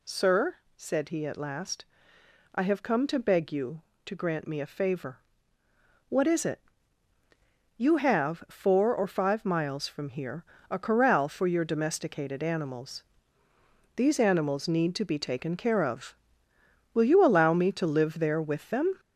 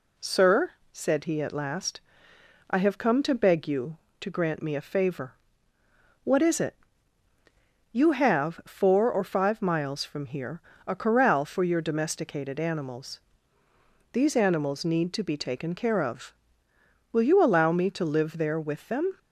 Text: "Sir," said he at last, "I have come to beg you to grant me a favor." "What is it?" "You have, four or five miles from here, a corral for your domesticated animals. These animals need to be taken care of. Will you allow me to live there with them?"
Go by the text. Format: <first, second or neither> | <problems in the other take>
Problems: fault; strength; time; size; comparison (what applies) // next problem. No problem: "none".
second | gets louder; noticeable; throughout; 4.5 dB